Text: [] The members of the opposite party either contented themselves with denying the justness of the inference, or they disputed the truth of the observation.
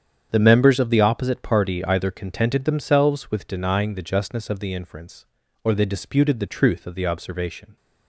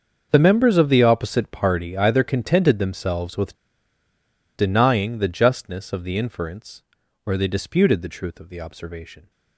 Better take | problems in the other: first | starts louder than the rest; until 1.3 s; 7 dB; strong in the first // pauses between "with" and "denying"; at 3.5 s; 0.99 s long

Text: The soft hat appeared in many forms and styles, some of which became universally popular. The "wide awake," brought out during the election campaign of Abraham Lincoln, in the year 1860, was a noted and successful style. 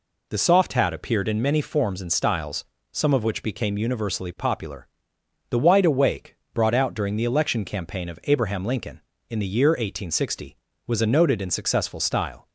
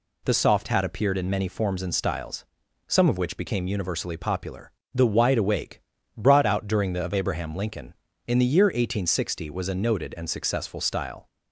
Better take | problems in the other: first | skips "election campaign"; at 7.0 s

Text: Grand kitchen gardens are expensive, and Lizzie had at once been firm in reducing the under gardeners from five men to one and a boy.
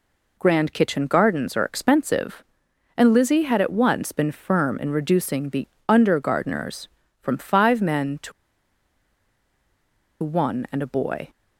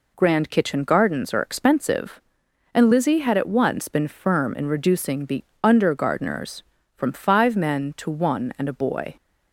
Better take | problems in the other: second | pauses between "the" and "under"; slight; at 5.6 s; 0.22 s long; slight in the second // pauses between "to" and "one"; strong; at 8.3 s; 1.9 s long

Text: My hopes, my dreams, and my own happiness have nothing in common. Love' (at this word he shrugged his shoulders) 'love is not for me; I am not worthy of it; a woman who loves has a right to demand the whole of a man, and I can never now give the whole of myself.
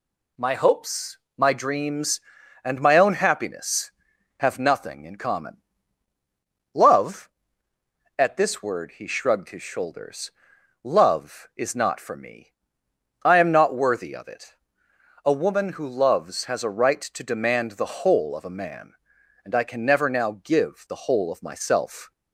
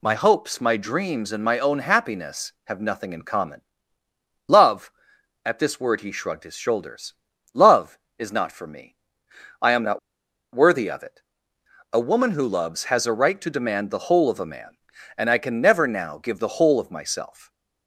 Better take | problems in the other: first | pauses between "not" and "worthy"; noticeable; at 9.9 s; 0.54 s long

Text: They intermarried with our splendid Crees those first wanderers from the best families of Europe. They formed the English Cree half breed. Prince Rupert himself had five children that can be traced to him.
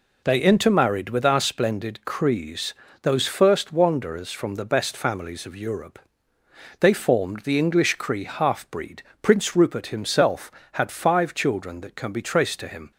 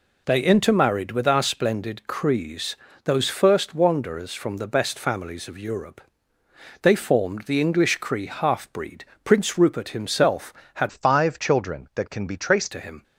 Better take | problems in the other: first | pauses between "Crees" and "those"; slight; at 2.7 s; 0.28 s long; slight in the first // changes voice from "five" to "traced"; from 10.8 to 12.7 s; 1.9 s long

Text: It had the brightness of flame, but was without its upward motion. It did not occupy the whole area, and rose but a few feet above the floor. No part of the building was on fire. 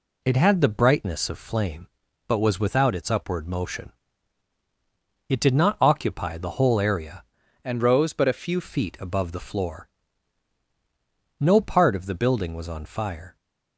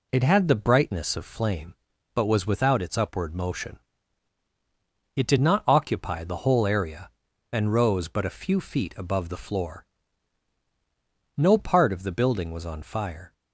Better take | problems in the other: second | changes voice from "and" to "few"; from 7.6 to 8.6 s; 1.0 s long

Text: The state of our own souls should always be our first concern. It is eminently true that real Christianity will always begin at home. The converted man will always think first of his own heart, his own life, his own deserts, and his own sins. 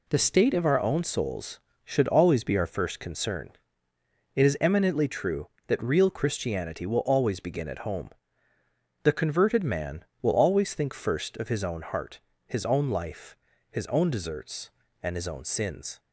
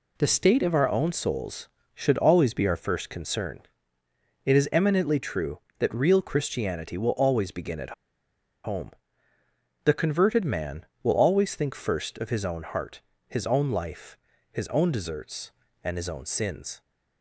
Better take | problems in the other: first | pauses between "at" and "home"; noticeable; at 7.9 s; 0.72 s long

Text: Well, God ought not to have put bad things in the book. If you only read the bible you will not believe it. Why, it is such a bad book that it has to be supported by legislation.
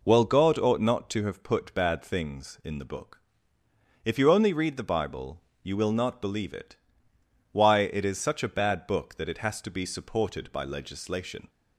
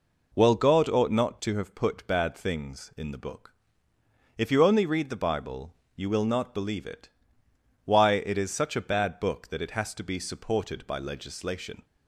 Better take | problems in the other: neither | pauses between "bible" and "you"; slight; the same in both

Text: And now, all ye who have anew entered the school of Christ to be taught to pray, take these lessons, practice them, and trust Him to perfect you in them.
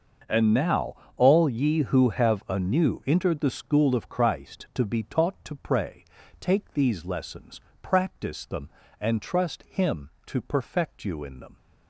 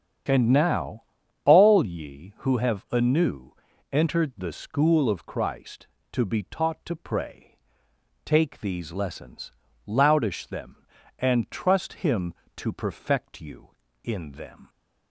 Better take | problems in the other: first | starts louder than the rest; strong; until 1.7 s; 8.5 dB; noticeable in the first // pauses between "anew" and "entered"; at 3.5 s; 0.38 s long // says "loudish" for "practice"; at 9.8 s

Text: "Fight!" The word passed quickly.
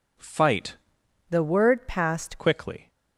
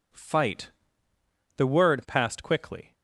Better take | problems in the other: second | changes voice from "The" to "passed"; from 1.2 to 2.3 s; 1.1 s long

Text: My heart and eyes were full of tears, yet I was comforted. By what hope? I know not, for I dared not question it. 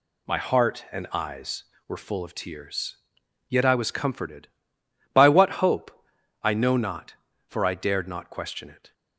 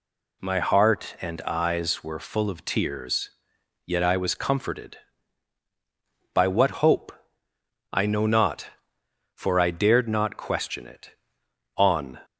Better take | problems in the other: first | goes on to say "On"; slight; from 11.7 s on; 0.42 s long

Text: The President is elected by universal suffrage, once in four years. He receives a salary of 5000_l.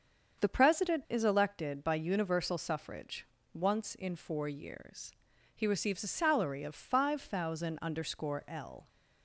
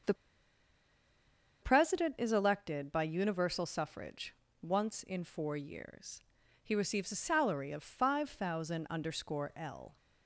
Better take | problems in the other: first | starts louder than the rest; strong; until 2.5 s; 7 dB; strong in the first // pauses between "The" and "President"; strong; at 0.1 s; 1.4 s long

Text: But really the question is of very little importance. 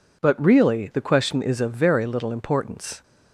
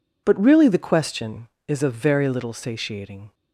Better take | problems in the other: first | says "satiating" for "importance"; at 2.5 s

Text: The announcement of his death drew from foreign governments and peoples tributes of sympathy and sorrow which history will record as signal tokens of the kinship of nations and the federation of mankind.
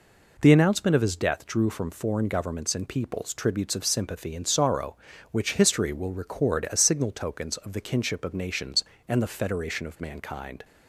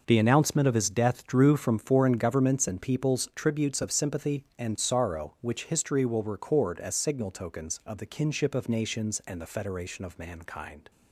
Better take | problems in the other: neither | none

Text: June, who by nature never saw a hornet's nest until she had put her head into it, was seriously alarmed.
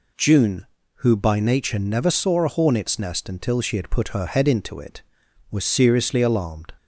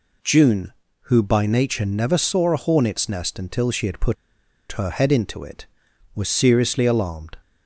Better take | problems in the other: first | pauses between "put" and "her"; noticeable; at 4.1 s; 0.57 s long

